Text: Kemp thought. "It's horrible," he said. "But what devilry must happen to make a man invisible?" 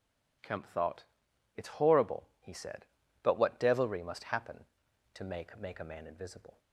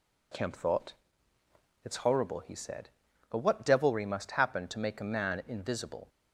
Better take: second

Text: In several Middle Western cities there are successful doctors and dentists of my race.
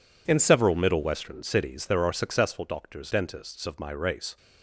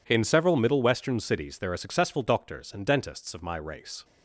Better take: second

